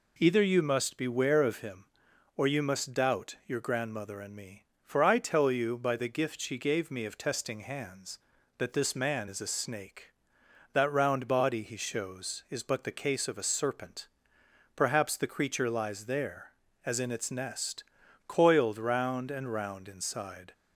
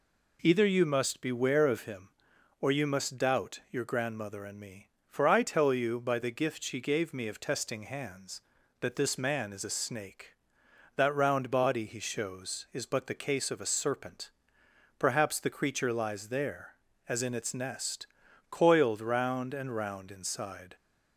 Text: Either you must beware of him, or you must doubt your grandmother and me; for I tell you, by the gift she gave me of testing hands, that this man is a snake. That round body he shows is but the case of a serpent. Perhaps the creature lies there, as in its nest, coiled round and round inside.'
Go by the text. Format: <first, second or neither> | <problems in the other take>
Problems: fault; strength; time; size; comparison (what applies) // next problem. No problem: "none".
neither | none